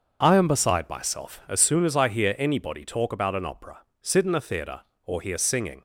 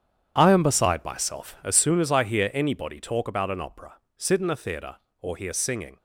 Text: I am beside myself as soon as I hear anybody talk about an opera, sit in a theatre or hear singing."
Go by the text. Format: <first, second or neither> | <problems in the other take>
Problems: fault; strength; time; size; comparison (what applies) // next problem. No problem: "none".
first | gets quieter; strong; throughout; 12.5 dB // starts louder than the rest; strong; until 1.3 s; 9 dB; also in the first